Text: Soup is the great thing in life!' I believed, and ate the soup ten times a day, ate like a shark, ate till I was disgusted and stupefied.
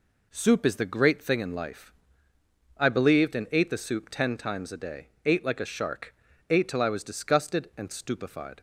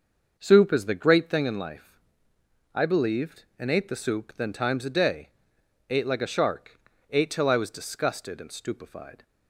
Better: first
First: none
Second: starts louder than the rest; until 1.3 s; 6.5 dB // says "then" for "ten"; at 4.3 s

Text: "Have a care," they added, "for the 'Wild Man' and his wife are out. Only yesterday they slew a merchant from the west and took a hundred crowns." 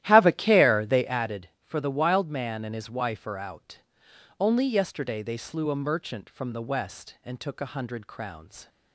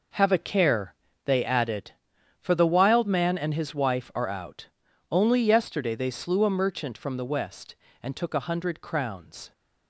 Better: second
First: starts louder than the rest; strong; until 1.3 s; 13.5 dB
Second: none

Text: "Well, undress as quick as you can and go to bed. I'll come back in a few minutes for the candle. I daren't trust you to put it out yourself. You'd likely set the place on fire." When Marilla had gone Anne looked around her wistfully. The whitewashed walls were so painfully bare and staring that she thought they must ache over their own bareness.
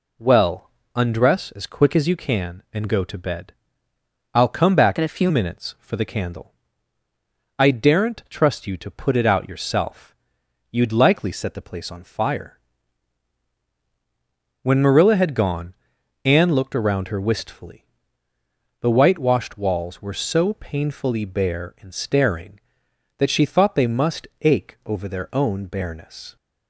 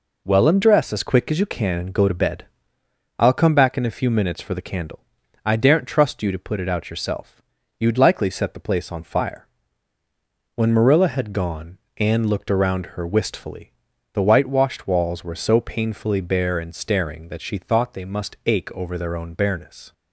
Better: second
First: changes voice from "in" to "few"; from 4.9 to 5.2 s; 0.3 s long // pauses between "gone" and "Anne"; noticeable; at 15.7 s; 0.50 s long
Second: pauses between "gone" and "Anne"; slight; at 11.7 s; 0.18 s long

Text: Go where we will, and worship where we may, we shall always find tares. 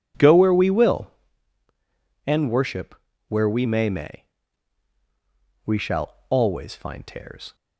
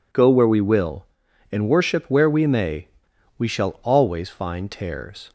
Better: second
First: pauses between "worship" and "where"; slight; at 2.9 s; 0.36 s long // says "may" twice; at 3.8 s // pauses between "shall" and "always"; slight; at 6.1 s; 0.16 s long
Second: none

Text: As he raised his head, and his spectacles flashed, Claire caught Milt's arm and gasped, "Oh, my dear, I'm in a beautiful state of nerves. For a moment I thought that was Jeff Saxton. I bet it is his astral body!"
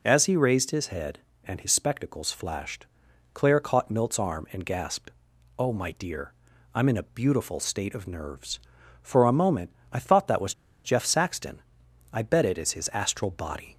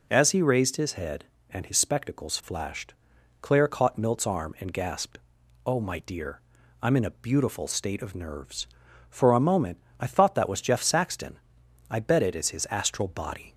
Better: second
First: pauses between "moment" and "I"; slight; at 9.7 s; 0.18 s long // pauses between "was" and "Jeff"; slight; at 10.5 s; 0.30 s long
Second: pauses between "moment" and "I"; slight; at 9.8 s; 0.18 s long

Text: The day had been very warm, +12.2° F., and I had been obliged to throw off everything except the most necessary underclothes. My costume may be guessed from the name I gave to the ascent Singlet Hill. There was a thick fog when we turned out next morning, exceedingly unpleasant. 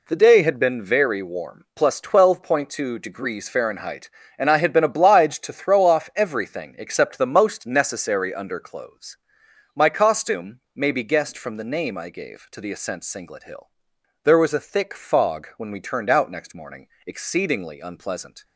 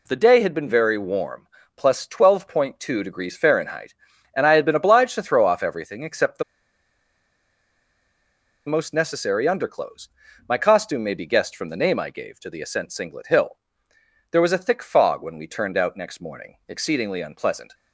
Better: first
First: none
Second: pauses between "the" and "most"; strong; at 6.4 s; 2.2 s long

